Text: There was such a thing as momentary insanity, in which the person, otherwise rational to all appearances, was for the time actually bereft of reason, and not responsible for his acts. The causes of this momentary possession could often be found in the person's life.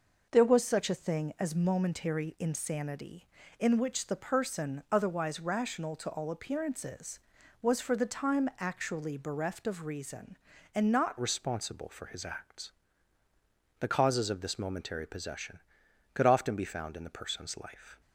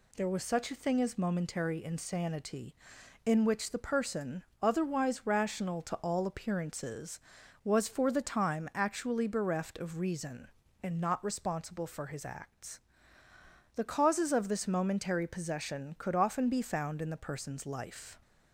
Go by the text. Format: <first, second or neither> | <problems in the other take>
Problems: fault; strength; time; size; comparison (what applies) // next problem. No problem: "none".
second | changes voice at "responsible"; from 11.2 s on; 6.8 s long